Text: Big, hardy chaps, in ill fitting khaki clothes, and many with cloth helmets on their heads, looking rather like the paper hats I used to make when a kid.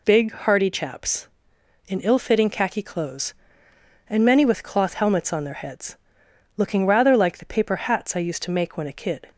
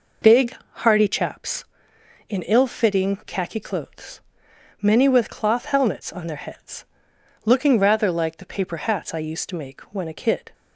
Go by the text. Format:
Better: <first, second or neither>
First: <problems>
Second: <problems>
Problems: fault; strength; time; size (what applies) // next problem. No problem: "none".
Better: first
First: none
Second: skips "and"; at 4.5 s